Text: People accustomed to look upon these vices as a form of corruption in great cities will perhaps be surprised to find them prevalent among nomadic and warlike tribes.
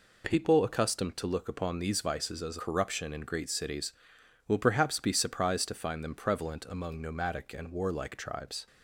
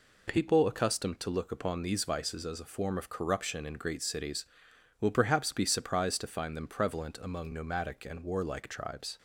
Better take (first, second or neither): second